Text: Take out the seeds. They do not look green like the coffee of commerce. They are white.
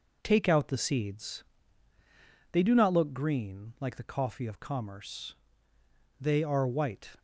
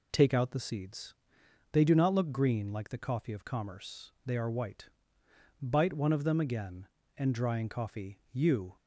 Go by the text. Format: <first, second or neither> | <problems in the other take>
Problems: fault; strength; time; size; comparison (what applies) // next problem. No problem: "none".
first | goes on to say "Bite one of them again and Drying Coffee you"; strong; from 5.6 s on; 3.1 s long